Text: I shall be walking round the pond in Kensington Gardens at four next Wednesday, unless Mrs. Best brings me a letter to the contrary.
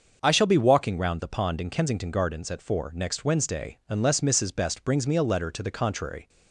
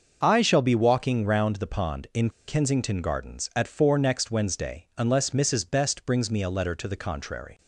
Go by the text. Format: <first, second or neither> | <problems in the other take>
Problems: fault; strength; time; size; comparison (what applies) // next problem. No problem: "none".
first | starts louder than the rest; until 1.2 s; 6 dB; also in the first // pauses between "in" and "Kensington"; slight; at 2.2 s; 0.17 s long